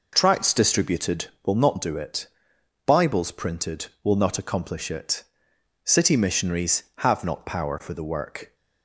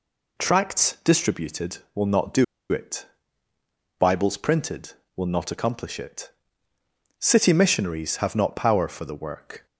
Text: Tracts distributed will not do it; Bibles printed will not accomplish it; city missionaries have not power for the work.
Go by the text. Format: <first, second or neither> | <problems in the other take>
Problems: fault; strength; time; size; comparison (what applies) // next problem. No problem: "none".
first | pauses between "do" and "it"; slight; at 2.4 s; 0.26 s long